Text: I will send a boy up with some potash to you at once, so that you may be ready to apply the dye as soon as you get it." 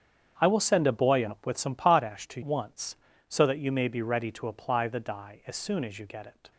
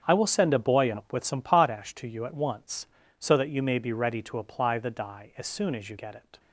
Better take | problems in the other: second | starts louder than the rest; strong; until 1.3 s; 8 dB; strong in the second // skips "you at"; at 2.4 s

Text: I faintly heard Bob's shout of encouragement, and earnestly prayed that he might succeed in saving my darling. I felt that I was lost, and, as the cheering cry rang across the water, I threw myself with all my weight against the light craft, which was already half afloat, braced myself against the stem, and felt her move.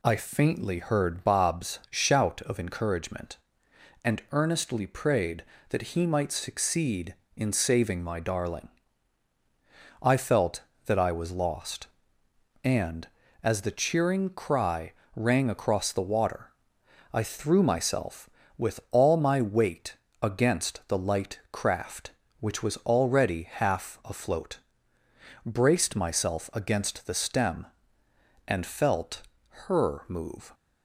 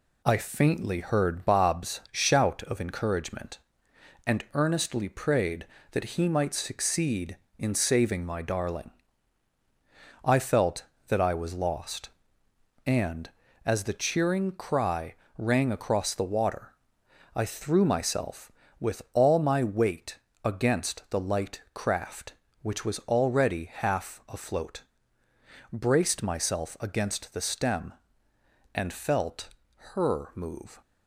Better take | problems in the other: first | gets quieter; noticeable; throughout; 4 dB // pauses between "cry" and "rang"; slight; at 15.1 s; 0.22 s long; slight in the first // pauses between "weight" and "against"; slight; at 20.1 s; 0.26 s long; slight in the first // pauses between "felt" and "her"; at 29.4 s; 0.44 s long; also in the first

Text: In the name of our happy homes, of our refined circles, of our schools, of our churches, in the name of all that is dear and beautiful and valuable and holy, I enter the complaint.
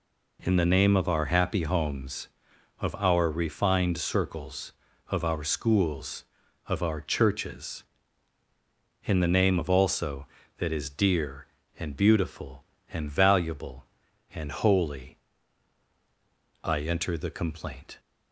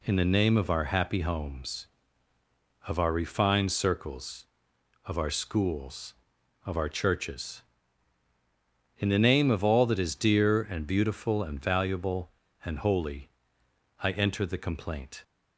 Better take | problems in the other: second | says "also" for "all"; at 9.6 s

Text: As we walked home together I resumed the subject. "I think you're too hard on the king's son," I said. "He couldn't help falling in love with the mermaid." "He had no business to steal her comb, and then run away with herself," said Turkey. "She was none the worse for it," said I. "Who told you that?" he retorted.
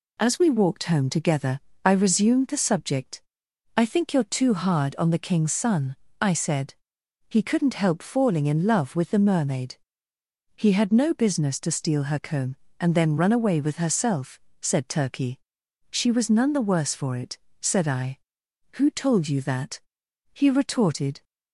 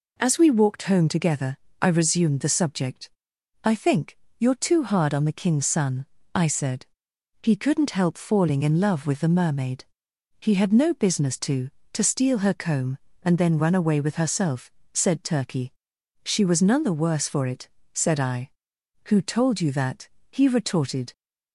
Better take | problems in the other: first | pauses between "together" and "I"; slight; at 1.5 s; 0.24 s long; slight in the first // pauses between "think" and "you're"; slight; at 4.1 s; 0.22 s long // says "to" twice; at 11.9 s

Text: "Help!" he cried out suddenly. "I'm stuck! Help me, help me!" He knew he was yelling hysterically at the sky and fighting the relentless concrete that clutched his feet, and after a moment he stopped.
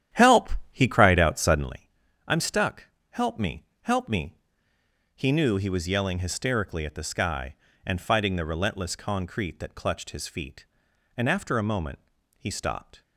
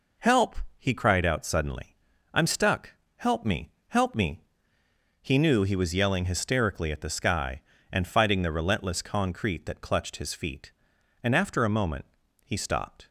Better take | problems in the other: second | starts louder than the rest; strong; until 1.7 s; 11 dB // pauses between "moment" and "he"; at 11.9 s; 0.38 s long; also in the second

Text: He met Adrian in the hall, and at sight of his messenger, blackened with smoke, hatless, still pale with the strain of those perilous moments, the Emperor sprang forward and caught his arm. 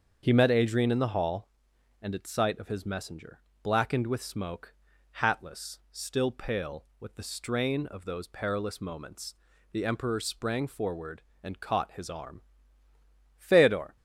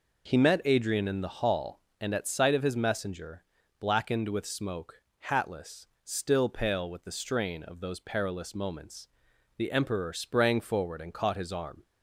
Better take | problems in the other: second | starts louder than the rest; until 1.2 s; 7 dB // goes on to say "Feodor"; from 13.3 s on; 0.60 s long

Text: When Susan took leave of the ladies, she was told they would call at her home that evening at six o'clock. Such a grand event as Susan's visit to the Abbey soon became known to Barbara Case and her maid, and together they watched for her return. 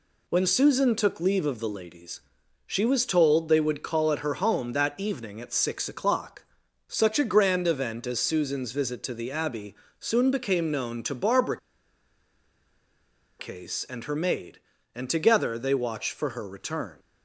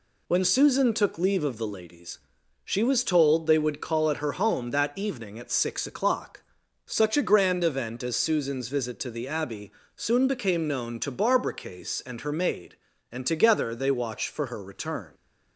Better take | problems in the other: second | pauses between "Abbey" and "soon"; slight; at 9.7 s; 0.28 s long; slight in the second // pauses between "Barbara" and "Case"; strong; at 11.5 s; 1.8 s long

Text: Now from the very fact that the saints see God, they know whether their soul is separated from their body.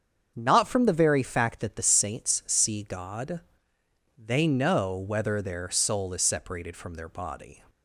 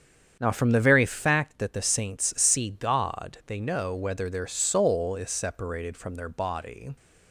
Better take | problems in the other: second | starts louder than the rest; strong; until 1.3 s; 7 dB; strong in the second // says "Not" for "Now"; at 0.3 s

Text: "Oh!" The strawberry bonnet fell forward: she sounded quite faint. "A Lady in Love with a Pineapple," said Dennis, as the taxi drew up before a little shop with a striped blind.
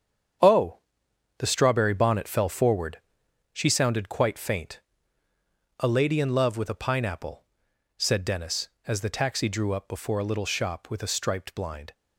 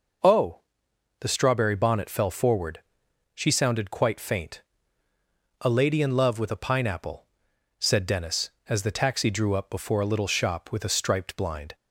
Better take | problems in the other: second | gets quieter; strong; throughout; 9 dB

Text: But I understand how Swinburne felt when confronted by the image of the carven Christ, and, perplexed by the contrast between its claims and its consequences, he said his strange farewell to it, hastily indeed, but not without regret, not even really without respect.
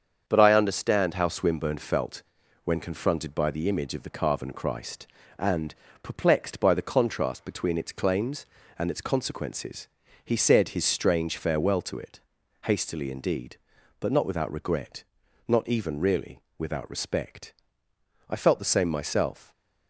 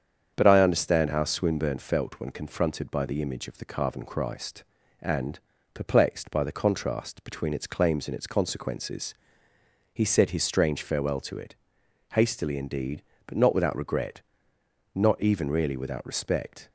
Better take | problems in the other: second | starts louder than the rest; strong; until 1.2 s; 7.5 dB; strong in the second // pauses between "felt" and "when"; at 2.2 s; 0.42 s long // pauses between "really" and "without"; slight; at 16.4 s; 0.18 s long // goes on to say "I felt the same myself"; noticeable; from 18.2 s on; 1.2 s long

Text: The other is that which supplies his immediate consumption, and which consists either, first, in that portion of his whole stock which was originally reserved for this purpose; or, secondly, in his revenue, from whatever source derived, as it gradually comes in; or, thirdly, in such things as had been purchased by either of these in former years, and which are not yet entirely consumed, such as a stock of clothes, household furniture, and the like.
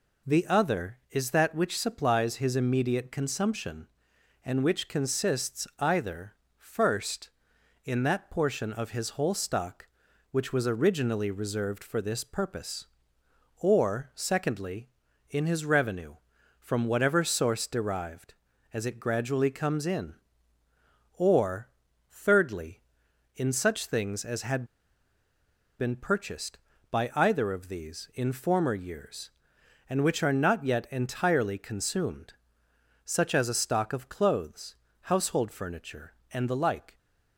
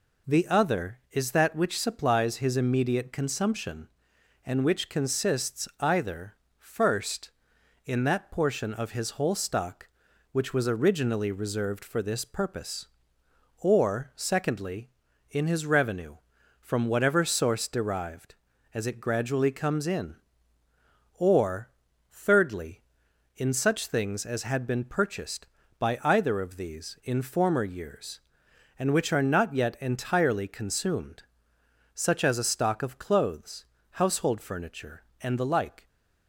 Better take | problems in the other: second | pauses between "had" and "been"; at 24.6 s; 1.1 s long

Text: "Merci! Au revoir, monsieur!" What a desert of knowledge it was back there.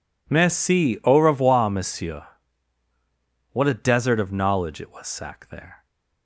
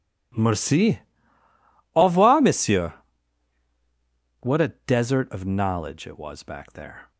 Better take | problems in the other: second | says "sack" for "back"; at 5.0 s

